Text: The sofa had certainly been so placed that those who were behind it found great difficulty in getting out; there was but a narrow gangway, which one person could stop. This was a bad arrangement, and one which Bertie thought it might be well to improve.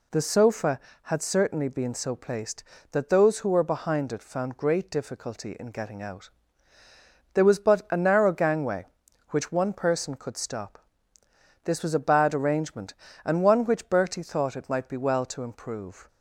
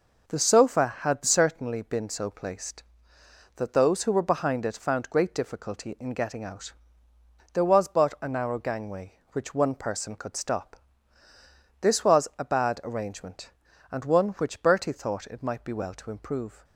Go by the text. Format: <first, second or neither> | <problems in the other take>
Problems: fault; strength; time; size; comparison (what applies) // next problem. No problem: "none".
neither | none